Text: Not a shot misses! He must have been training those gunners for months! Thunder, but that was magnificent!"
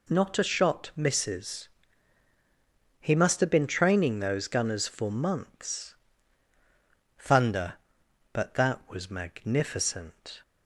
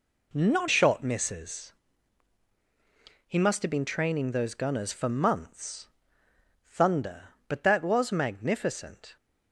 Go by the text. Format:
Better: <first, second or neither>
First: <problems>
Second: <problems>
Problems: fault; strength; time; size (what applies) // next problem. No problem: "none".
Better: first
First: none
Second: skips "a"; at 0.6 s